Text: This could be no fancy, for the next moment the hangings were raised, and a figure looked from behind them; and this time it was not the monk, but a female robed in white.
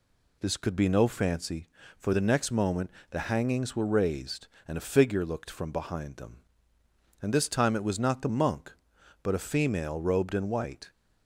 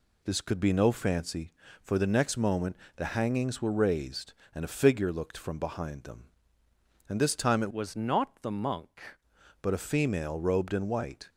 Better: first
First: pauses between "moment" and "the"; slight; at 2.9 s; 0.20 s long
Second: pauses between "moment" and "the"; slight; at 2.7 s; 0.20 s long // changes voice from "was" to "monk"; from 7.7 to 9.1 s; 1.4 s long

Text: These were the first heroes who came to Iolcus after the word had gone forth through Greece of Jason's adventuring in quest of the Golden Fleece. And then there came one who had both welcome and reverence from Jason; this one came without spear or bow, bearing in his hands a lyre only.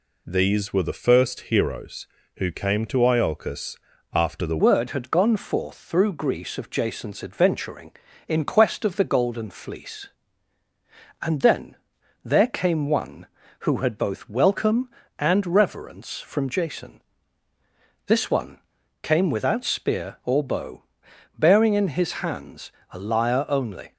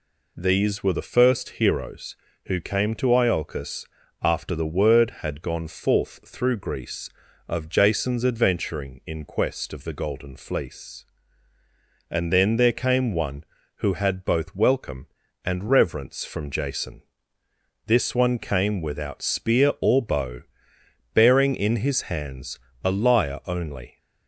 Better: second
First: pauses between "Iolcus" and "after"; at 3.7 s; 0.38 s long // changes voice at "word"; from 4.5 s on; 19.4 s long // pauses between "then" and "there"; noticeable; at 11.7 s; 0.48 s long // pauses between "one" and "came"; at 18.5 s; 0.44 s long // pauses between "hands" and "a"; slight; at 22.7 s; 0.18 s long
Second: pauses between "Iolcus" and "after"; at 3.8 s; 0.38 s long // pauses between "hands" and "a"; slight; at 22.5 s; 0.28 s long

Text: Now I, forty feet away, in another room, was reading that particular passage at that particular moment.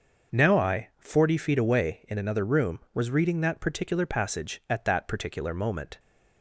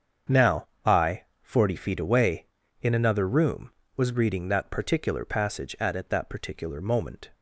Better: first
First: starts louder than the rest; until 1.4 s; 6 dB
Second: starts louder than the rest; strong; until 1.6 s; 7.5 dB // pauses between "Now" and "I"; slight; at 0.6 s; 0.18 s long // says "at" twice; at 5.9 s

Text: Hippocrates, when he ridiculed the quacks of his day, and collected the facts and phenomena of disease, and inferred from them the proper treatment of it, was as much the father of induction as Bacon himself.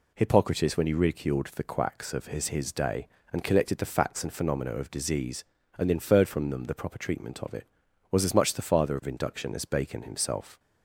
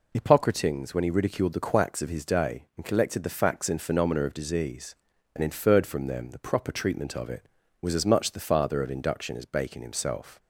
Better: second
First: says "his" twice; at 2.4 s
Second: none

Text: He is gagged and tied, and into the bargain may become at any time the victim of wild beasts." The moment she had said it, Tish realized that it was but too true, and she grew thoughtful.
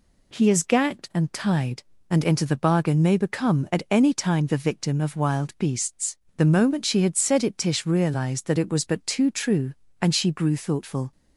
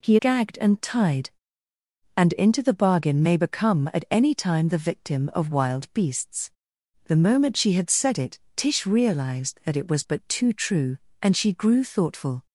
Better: first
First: none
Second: skips "is"; at 0.1 s

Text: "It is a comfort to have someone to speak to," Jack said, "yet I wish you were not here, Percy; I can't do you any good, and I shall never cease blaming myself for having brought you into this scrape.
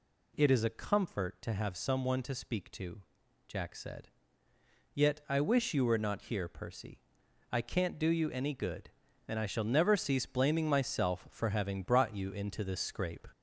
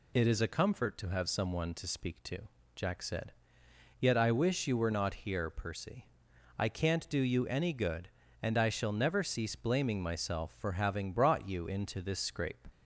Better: second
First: gets louder; slight; throughout; 3 dB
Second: none

